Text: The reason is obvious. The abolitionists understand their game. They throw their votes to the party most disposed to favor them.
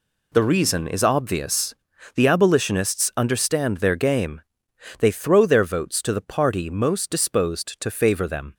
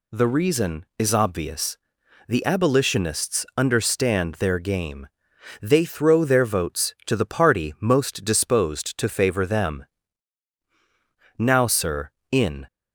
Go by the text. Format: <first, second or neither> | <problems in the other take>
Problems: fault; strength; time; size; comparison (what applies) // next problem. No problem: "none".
first | goes on to say "Now sir in"; noticeable; from 11.3 s on; 1.2 s long